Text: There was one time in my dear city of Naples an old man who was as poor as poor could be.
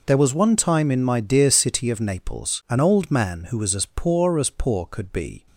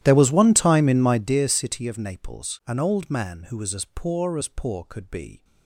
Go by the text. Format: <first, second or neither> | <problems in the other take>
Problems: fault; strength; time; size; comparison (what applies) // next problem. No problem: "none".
first | starts louder than the rest; strong; until 1.4 s; 12.5 dB